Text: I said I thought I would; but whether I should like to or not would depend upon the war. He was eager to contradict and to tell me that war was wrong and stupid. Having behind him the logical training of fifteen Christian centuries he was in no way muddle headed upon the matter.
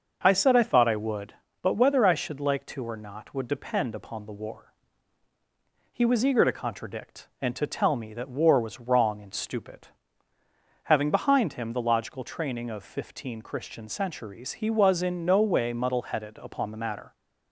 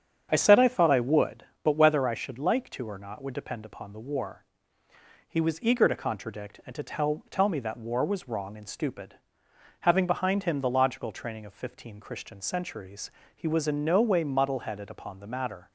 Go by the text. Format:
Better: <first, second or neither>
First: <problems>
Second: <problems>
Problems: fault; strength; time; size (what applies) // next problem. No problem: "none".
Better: first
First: starts louder than the rest; until 1.2 s; 6.5 dB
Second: starts louder than the rest; strong; until 1.3 s; 8 dB // says "tell" twice; at 7.3 s // pauses between "centuries" and "he"; slight; at 13.0 s; 0.26 s long